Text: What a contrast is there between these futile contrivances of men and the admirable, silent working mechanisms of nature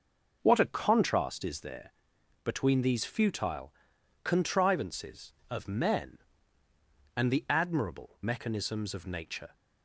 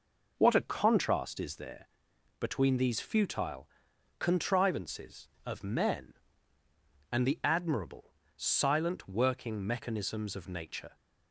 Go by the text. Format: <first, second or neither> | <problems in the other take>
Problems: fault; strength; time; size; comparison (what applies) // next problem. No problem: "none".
second | starts louder than the rest; noticeable; until 1.4 s; 6 dB // pauses between "there" and "between"; noticeable; at 1.9 s; 0.54 s long; noticeable in the second // pauses between "futile" and "contrivances"; noticeable; at 3.7 s; 0.50 s long; noticeable in the second // skips "silent working"; at 8.2 s